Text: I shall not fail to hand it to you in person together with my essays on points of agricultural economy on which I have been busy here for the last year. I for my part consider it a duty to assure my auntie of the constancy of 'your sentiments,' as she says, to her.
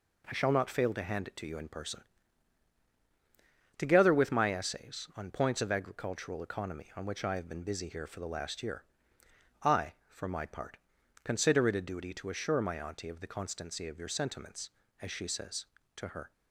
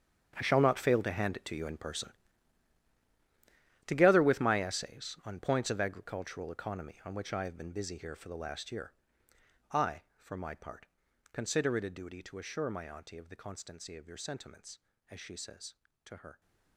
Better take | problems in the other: first | gets quieter; strong; throughout; 15.5 dB // pauses between "person" and "together"; strong; at 2.1 s; 1.7 s long; strong in the first // pauses between "part" and "consider"; noticeable; at 10.8 s; 0.46 s long; noticeable in the first

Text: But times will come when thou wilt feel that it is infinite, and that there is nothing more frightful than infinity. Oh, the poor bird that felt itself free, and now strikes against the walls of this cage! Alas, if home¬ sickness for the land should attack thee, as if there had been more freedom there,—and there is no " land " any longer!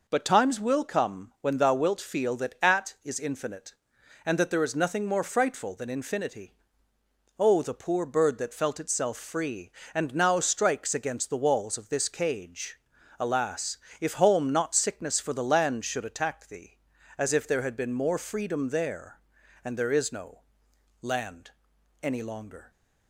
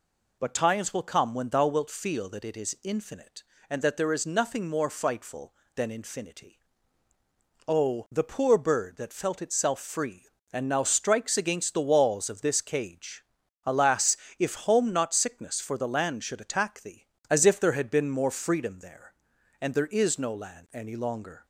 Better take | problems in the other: second | says "at" for "it"; at 2.6 s

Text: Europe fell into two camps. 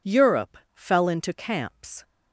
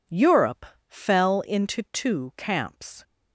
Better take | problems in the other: second | pauses between "Europe" and "fell"; slight; at 0.5 s; 0.18 s long; slight in the second // skips "two"; at 1.3 s

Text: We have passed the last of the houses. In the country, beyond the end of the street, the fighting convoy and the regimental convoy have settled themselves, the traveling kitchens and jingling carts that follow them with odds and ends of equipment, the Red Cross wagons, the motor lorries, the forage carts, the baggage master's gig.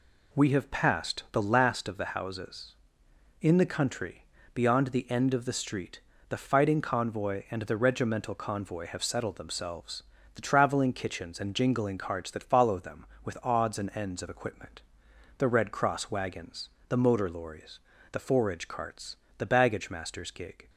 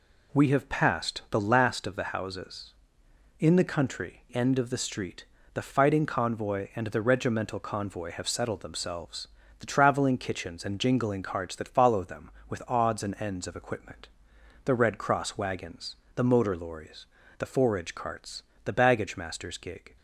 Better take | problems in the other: first | skips "beyond the"; at 4.3 s

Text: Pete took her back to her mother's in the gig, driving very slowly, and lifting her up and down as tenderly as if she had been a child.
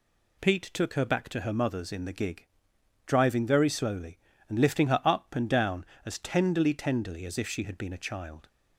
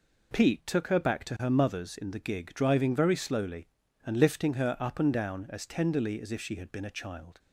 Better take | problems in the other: second | says "tenderly" twice; at 6.7 s

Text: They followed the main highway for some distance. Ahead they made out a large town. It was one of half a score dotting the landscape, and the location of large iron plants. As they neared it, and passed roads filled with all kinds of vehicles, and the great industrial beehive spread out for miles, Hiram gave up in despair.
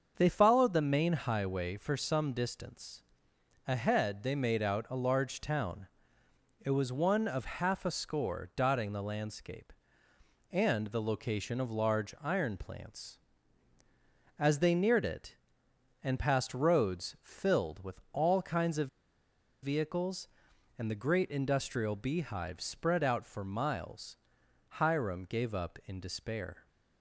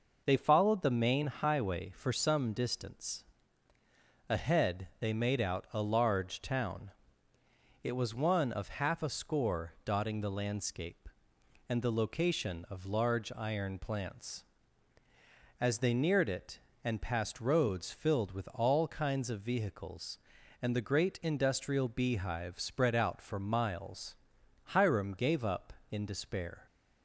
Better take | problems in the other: second | starts louder than the rest; until 1.1 s; 6.5 dB // pauses between "of" and "vehicles"; noticeable; at 18.8 s; 0.75 s long

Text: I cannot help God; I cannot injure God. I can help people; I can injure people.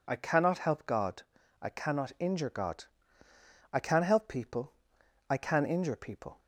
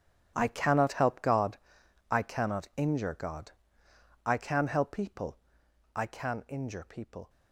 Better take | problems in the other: first | gets quieter; strong; throughout; 16 dB

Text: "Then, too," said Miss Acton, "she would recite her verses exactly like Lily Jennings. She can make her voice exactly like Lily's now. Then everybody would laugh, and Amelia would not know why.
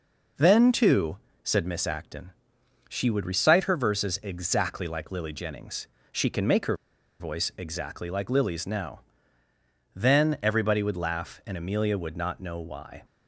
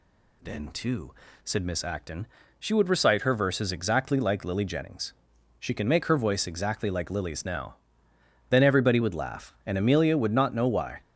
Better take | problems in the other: second | pauses between "her" and "voice"; at 6.7 s; 0.43 s long

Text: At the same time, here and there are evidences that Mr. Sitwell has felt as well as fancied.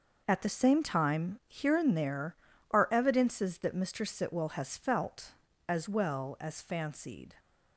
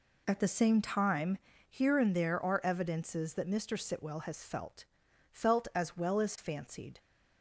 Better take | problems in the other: first | says "felt" twice; at 5.3 s

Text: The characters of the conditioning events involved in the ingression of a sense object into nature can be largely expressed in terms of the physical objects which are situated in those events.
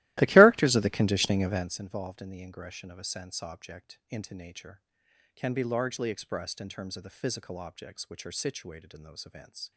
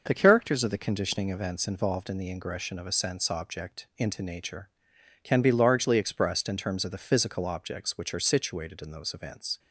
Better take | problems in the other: second | starts louder than the rest; strong; until 1.8 s; 17 dB

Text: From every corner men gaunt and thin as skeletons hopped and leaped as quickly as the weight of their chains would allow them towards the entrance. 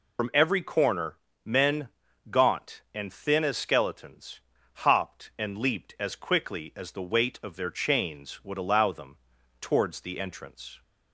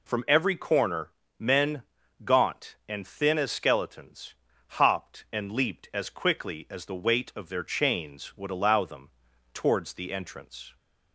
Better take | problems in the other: second | loses the start of "From"; at 0.1 s; 65 ms // pauses between "corner" and "men"; slight; at 1.1 s; 0.26 s long; slight in the second // pauses between "men" and "gaunt"; at 1.8 s; 0.40 s long; also in the second // pauses between "skeletons" and "hopped"; at 4.4 s; 0.44 s long; also in the second // pauses between "them" and "towards"; at 9.1 s; 0.42 s long; also in the second

